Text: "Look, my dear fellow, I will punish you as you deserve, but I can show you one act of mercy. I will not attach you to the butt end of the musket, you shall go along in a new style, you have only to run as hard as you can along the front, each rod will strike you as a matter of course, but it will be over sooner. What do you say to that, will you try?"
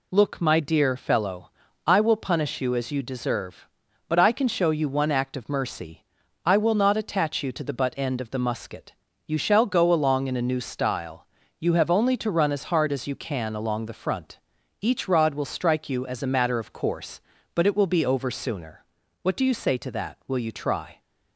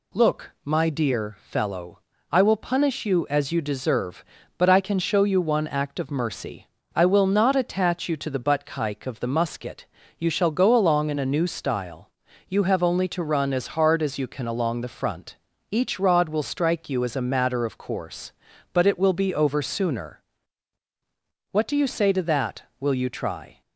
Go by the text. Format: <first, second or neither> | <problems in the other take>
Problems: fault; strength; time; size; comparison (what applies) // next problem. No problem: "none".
first | says "kike" for "end"; at 8.6 s